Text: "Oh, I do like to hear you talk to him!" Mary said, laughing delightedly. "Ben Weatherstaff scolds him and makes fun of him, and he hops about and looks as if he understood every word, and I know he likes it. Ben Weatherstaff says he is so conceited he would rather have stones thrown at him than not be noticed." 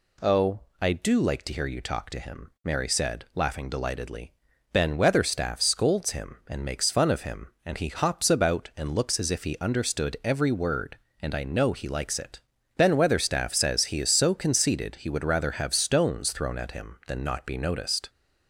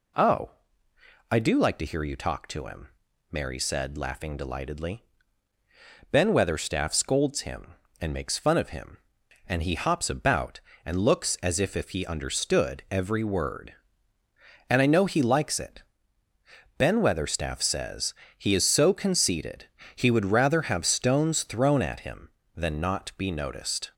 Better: first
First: none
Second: says "if" twice; at 11.7 s // pauses between "says" and "he"; slight; at 18.1 s; 0.24 s long // pauses between "conceited" and "he"; slight; at 19.6 s; 0.30 s long

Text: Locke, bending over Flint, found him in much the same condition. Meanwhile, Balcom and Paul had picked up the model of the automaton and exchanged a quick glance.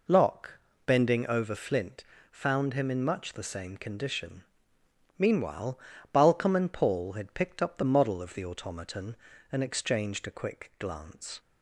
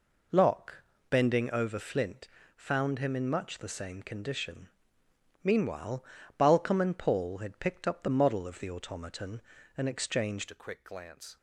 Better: first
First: none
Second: changes voice at "a"; from 10.5 s on; 0.8 s long

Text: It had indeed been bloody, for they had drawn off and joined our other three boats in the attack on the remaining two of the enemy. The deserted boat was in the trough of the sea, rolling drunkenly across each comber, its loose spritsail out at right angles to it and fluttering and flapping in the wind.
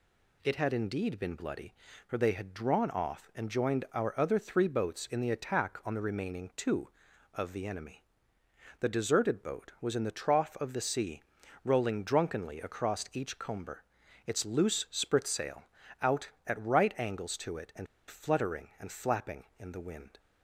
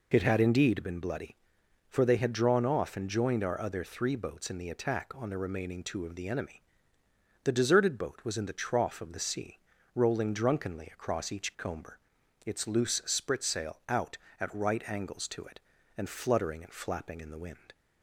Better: second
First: pauses between "spritsail" and "out"; at 15.6 s; 0.38 s long // pauses between "and" and "fluttering"; slight; at 17.8 s; 0.22 s long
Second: none

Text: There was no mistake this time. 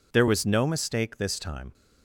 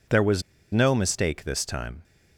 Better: first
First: none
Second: pauses between "was" and "no"; slight; at 0.4 s; 0.30 s long

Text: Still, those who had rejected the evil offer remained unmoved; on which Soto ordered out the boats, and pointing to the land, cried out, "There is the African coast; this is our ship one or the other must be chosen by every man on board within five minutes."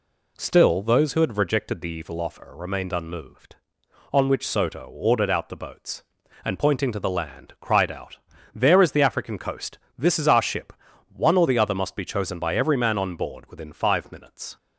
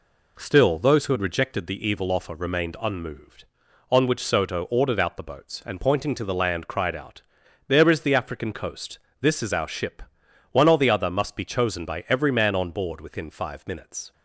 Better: neither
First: pauses between "ship" and "one"; at 10.7 s; 0.42 s long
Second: pauses between "ship" and "one"; noticeable; at 10.0 s; 0.48 s long

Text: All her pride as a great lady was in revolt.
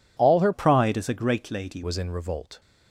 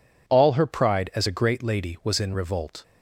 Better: second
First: changes voice from "pride" to "lady"; from 0.5 to 1.8 s; 1.3 s long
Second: none

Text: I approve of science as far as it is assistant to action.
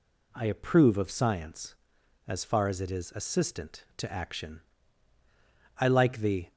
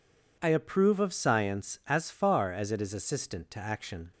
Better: second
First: goes on to say "I like the"; noticeable; from 5.7 s on; 0.72 s long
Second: none

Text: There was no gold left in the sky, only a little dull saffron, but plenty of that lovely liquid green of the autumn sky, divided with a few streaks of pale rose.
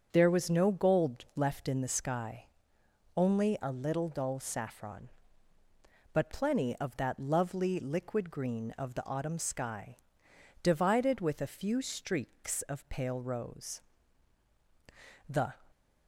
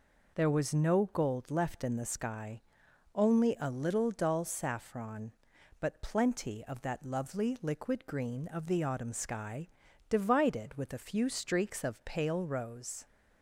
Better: second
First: starts louder than the rest; until 1.1 s; 7 dB // goes on to say "The"; slight; from 15.2 s on; 0.30 s long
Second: none

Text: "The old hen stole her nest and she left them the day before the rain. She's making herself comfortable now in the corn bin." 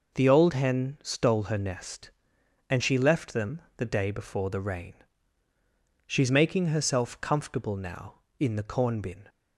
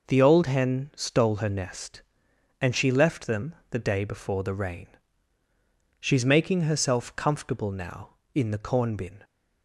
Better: neither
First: pauses between "them" and "the"; slight; at 3.6 s; 0.16 s long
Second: pauses between "them" and "the"; slight; at 3.5 s; 0.16 s long

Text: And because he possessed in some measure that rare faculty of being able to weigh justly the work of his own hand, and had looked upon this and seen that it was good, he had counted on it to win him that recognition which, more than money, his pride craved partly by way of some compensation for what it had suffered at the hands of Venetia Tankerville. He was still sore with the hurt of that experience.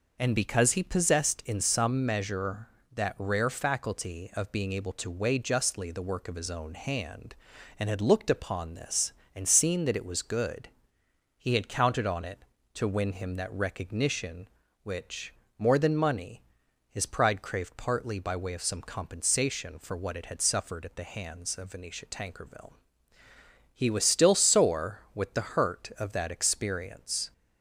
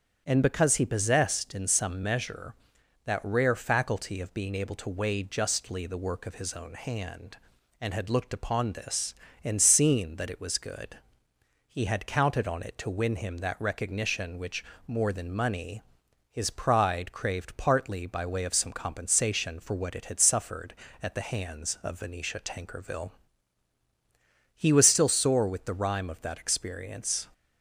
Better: first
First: none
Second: starts louder than the rest; strong; until 1.2 s; 8 dB // says "rhyme" for "hurt"; at 25.7 s

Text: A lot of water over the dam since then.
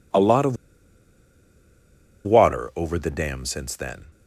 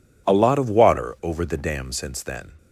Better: second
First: pauses between "of" and "water"; strong; at 0.5 s; 1.6 s long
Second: none

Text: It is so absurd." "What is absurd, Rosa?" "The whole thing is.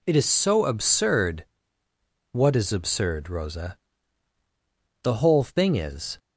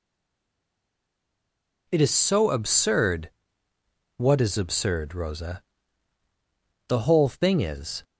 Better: first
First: none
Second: stays silent before the first word; noticeable; until 1.8 s; 1.8 s long

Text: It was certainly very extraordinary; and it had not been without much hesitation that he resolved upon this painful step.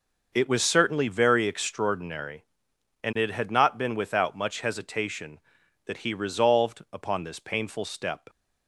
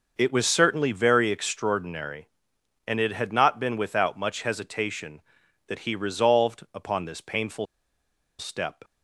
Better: first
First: none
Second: pauses between "painful" and "step"; noticeable; at 7.6 s; 0.74 s long

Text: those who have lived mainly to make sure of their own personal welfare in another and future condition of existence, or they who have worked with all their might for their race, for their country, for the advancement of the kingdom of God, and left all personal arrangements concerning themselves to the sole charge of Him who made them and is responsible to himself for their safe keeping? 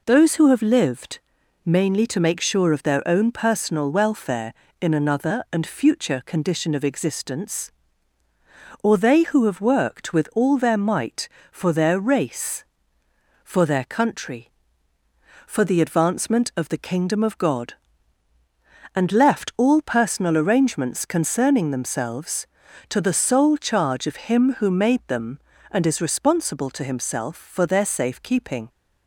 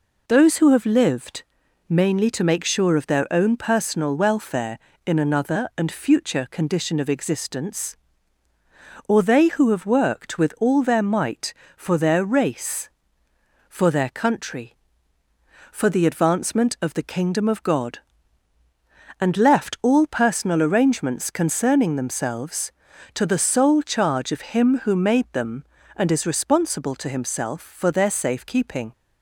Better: neither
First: pauses between "lived" and "mainly"; at 1.1 s; 0.44 s long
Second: pauses between "lived" and "mainly"; at 1.4 s; 0.44 s long

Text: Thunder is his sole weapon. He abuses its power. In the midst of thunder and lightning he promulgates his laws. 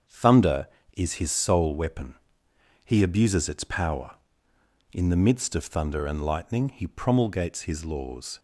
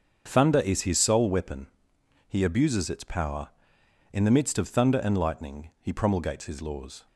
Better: neither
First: starts louder than the rest; until 1.3 s; 7 dB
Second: starts louder than the rest; until 1.2 s; 6.5 dB

